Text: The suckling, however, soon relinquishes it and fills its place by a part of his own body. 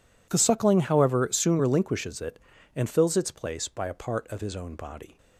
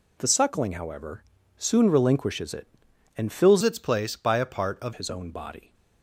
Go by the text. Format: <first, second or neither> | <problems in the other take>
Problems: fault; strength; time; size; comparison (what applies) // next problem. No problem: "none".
first | changes voice from "its" to "of"; from 3.6 to 4.9 s; 1.3 s long